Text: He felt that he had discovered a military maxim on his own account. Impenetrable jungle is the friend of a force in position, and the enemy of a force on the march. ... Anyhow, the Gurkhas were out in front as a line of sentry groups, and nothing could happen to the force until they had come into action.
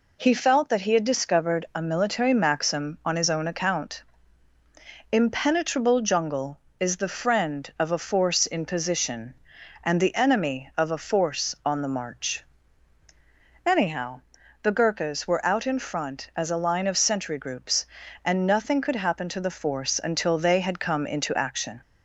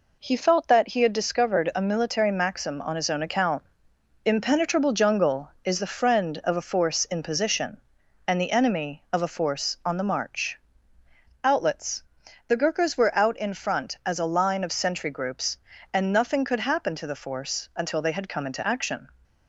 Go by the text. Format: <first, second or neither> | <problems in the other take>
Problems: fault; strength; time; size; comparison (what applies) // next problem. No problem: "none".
first | says "Outlets" for "Anyhow"; at 11.4 s